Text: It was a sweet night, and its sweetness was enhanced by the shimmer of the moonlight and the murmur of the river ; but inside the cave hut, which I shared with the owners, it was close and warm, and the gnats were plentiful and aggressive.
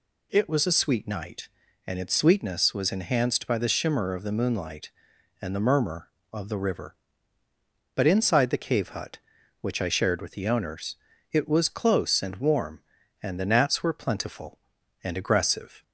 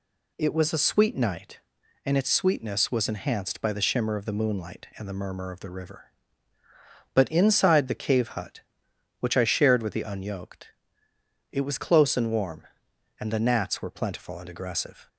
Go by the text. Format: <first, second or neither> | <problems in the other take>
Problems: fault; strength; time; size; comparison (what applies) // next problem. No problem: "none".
first | says "unyoked" for "owners"; at 10.0 s